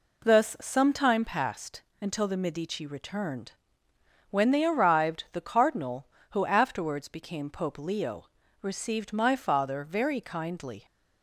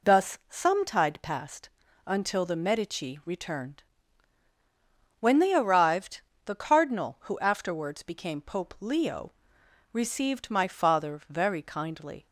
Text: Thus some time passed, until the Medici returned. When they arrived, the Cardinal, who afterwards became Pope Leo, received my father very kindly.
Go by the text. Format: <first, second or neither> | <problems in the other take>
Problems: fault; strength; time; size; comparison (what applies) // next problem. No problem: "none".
first | says "tide" for "time"; at 0.8 s